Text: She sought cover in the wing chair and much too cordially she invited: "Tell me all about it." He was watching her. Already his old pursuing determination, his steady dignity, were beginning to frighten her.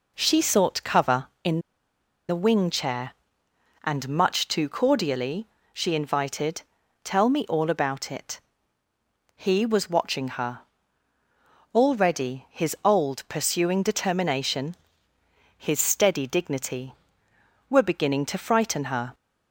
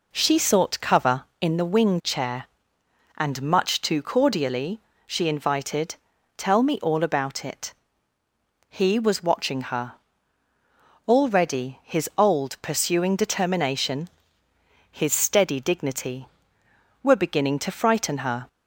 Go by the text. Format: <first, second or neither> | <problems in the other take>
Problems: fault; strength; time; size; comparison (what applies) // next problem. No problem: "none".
second | pauses between "in" and "the"; noticeable; at 1.5 s; 0.70 s long // pauses between "cordially" and "she"; slight; at 5.4 s; 0.26 s long; slight in the second